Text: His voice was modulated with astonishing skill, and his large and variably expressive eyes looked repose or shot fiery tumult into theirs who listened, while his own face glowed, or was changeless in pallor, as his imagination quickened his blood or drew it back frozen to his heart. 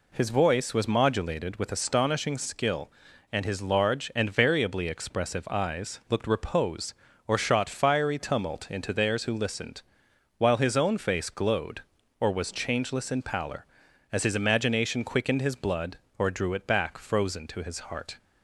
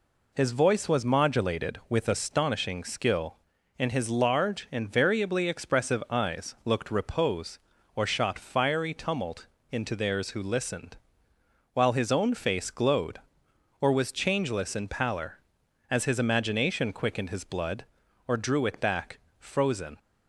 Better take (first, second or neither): first